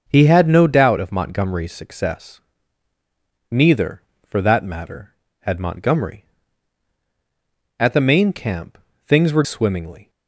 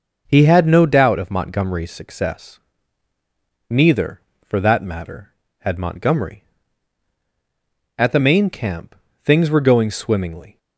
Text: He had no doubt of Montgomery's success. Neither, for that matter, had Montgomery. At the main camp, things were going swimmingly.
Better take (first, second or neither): second